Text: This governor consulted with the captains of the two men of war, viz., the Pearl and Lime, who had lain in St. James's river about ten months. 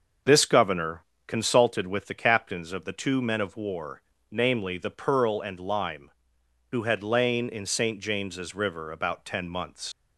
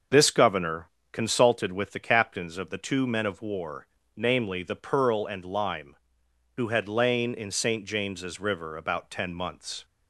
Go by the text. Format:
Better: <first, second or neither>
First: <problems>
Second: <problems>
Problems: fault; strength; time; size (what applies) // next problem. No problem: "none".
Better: second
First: starts louder than the rest; until 1.4 s; 6.5 dB // pauses between "governor" and "consulted"; slight; at 1.0 s; 0.22 s long // leaves "months" unfinished; at 9.9 s; 75 ms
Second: starts louder than the rest; until 1.3 s; 6.5 dB // pauses between "governor" and "consulted"; slight; at 0.8 s; 0.22 s long